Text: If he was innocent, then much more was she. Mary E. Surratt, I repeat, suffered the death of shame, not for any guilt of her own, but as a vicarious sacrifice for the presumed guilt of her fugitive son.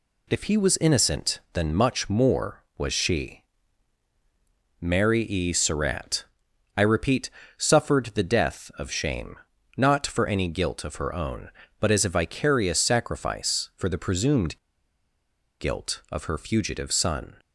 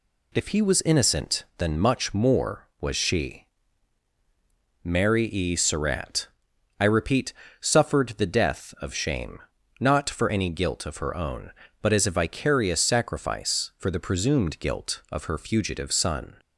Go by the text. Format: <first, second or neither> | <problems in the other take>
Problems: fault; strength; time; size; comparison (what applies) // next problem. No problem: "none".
second | pauses between "presumed" and "guilt"; at 14.5 s; 1.0 s long